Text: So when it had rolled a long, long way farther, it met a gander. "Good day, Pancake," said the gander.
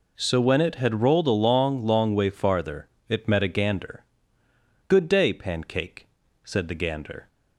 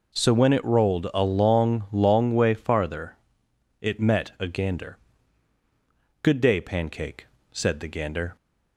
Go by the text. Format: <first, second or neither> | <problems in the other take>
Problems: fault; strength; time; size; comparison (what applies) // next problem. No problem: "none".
first | skips "had"; at 0.6 s